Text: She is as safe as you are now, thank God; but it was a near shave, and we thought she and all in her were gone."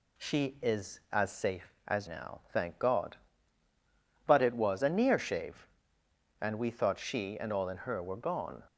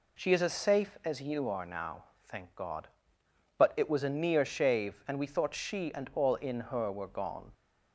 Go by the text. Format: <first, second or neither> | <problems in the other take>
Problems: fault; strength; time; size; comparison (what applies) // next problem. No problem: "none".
second | skips "you are"; at 2.0 s